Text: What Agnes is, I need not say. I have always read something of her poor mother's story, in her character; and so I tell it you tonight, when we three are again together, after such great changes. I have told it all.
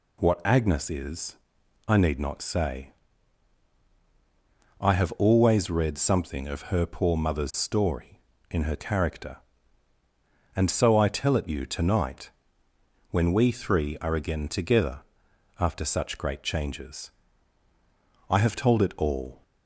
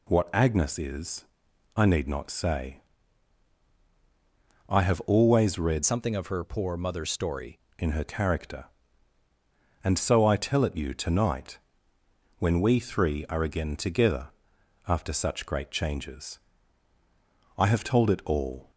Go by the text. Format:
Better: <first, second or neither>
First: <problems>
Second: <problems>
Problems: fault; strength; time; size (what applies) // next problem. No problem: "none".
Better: first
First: none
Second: changes voice from "something" to "story"; from 5.8 to 7.5 s; 1.7 s long